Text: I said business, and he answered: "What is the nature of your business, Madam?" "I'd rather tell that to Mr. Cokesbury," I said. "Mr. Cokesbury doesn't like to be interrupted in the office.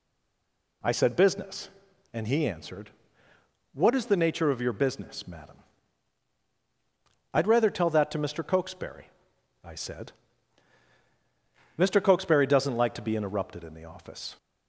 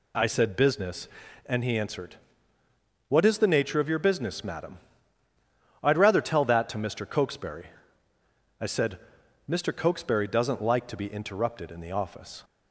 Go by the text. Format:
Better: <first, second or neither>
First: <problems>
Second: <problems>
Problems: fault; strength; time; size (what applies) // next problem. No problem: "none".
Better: second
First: stays silent before the first word; slight; until 0.8 s; 0.8 s long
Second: none